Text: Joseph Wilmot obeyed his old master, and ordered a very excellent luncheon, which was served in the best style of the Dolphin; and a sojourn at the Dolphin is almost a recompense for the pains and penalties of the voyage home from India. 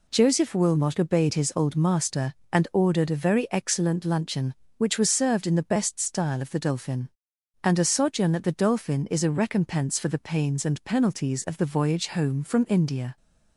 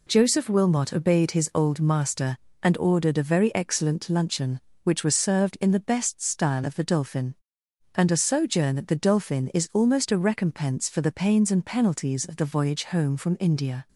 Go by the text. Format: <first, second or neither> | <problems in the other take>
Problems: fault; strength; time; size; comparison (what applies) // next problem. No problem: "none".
second | skips "almost"; at 9.2 s